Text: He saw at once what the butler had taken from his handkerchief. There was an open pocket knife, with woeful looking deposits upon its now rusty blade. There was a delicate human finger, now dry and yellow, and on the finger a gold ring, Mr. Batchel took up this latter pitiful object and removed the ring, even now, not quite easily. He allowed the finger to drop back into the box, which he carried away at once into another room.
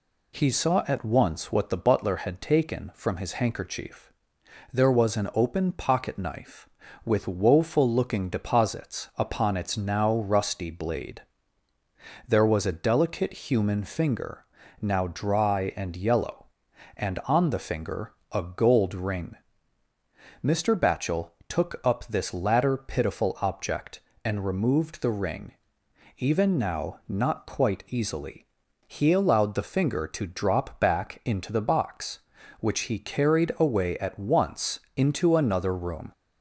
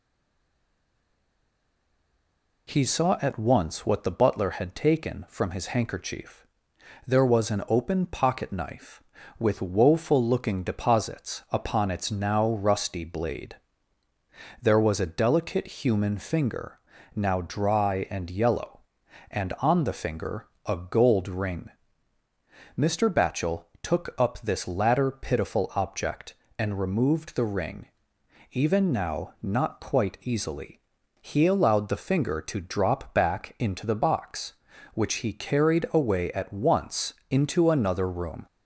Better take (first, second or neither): first